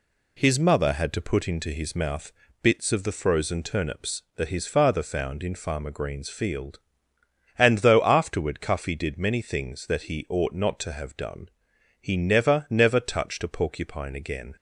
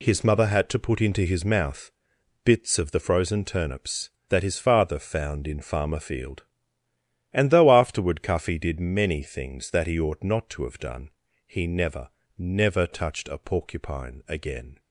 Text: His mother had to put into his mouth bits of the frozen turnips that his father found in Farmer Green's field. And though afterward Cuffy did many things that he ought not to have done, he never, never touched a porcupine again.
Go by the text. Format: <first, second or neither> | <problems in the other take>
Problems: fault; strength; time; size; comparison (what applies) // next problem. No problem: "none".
first | pauses between "mouth" and "bits"; noticeable; at 1.9 s; 0.52 s long; slight in the first // skips "Green's"; at 5.9 s